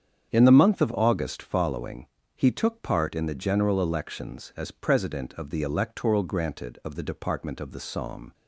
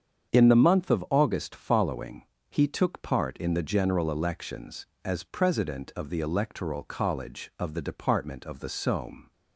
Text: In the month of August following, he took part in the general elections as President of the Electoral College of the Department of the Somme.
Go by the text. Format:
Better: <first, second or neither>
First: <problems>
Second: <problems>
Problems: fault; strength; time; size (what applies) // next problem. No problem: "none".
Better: second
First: starts louder than the rest; strong; until 1.3 s; 8 dB // says "Granted" for "College"; at 6.2 s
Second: starts louder than the rest; strong; until 1.3 s; 7.5 dB